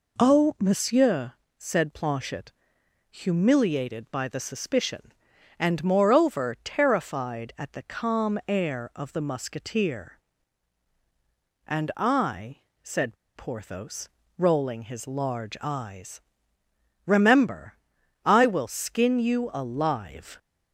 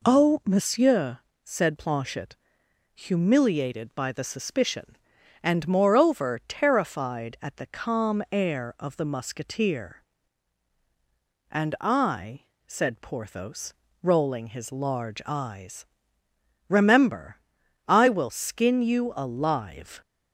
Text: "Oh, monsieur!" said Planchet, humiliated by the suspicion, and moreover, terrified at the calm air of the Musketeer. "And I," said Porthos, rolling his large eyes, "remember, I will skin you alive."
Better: second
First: pauses between "said" and "Porthos"; slight; at 13.1 s; 0.22 s long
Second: none

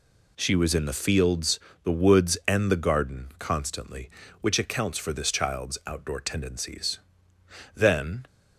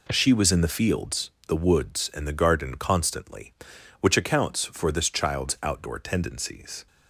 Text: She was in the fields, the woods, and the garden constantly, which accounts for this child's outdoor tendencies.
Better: second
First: goes on to say "Then"; from 7.7 s on; 0.52 s long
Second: none

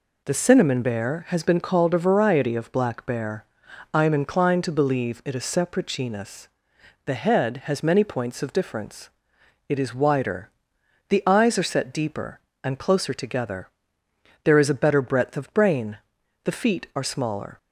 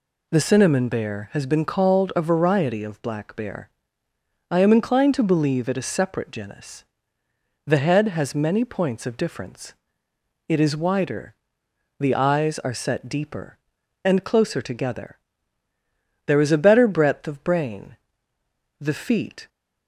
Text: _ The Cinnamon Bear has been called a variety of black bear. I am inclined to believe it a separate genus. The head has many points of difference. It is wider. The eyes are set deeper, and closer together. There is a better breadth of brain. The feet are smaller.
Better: first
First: none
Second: stops before "are smaller"; at 19.4 s

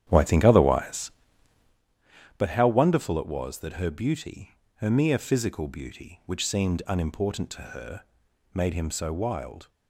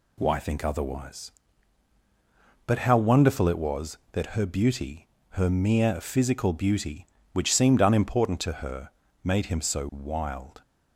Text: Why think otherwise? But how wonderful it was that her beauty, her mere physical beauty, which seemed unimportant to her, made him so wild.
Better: second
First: starts louder than the rest; strong; until 1.8 s; 10.5 dB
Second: none

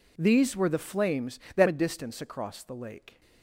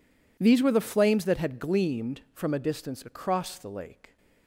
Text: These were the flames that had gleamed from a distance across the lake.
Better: second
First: skips "had gleamed from"; at 1.6 s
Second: none

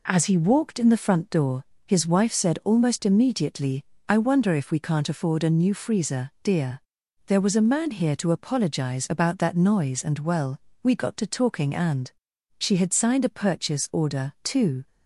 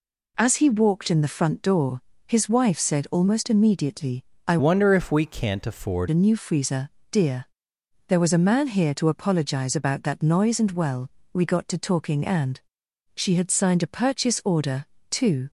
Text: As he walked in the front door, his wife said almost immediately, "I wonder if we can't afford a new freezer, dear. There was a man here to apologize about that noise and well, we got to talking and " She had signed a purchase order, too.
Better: first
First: none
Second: changes voice from "wonder" to "afford"; from 4.5 to 6.0 s; 1.5 s long

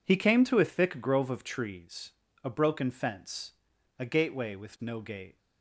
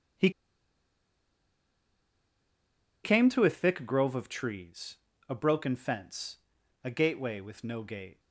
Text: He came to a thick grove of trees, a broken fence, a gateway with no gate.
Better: first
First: none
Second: pauses between "He" and "came"; strong; at 0.2 s; 2.7 s long

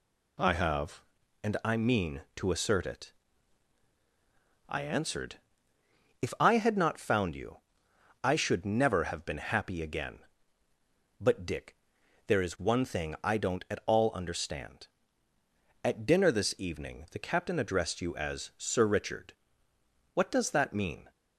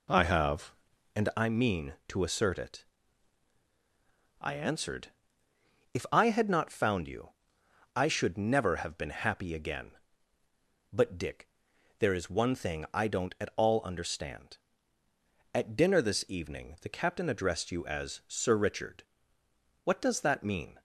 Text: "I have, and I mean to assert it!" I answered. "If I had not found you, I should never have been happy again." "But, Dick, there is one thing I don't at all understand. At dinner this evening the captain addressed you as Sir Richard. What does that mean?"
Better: first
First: none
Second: starts louder than the rest; until 1.5 s; 3.5 dB

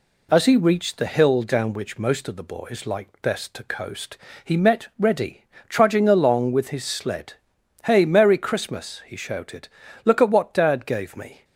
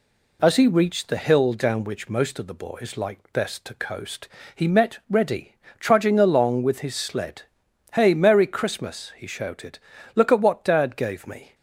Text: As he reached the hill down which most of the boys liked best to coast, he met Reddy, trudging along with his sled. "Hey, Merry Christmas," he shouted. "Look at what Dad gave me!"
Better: neither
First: none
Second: none

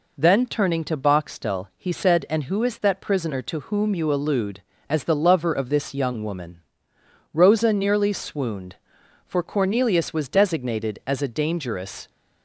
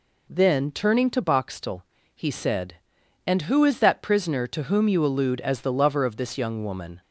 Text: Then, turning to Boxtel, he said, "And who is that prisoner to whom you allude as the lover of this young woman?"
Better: second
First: goes on to say "Rosa nearly swooned for Cornelius was designated as a dangerous"; strong; from 7.3 s on; 4.7 s long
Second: none

